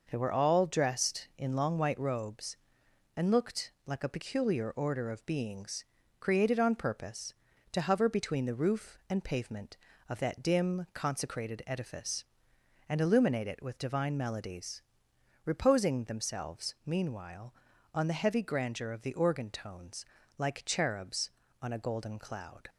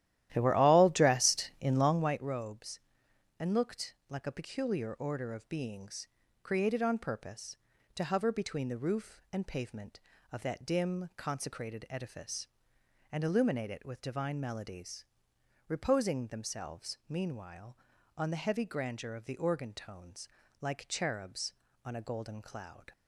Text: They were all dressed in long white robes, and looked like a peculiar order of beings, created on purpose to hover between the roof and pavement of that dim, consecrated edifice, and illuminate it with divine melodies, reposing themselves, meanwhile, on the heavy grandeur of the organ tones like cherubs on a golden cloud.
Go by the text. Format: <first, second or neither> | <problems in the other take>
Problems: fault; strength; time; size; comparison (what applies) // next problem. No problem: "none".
first | starts louder than the rest; strong; until 2.2 s; 13 dB // pauses between "tones" and "like"; slight; at 20.2 s; 0.32 s long; slight in the first